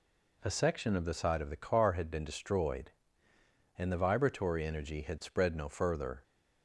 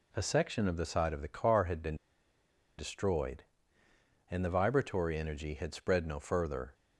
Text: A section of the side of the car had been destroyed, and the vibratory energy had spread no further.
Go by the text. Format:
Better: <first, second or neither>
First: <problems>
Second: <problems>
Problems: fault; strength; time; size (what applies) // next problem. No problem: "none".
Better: first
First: none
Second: pauses between "been" and "destroyed"; noticeable; at 1.9 s; 0.83 s long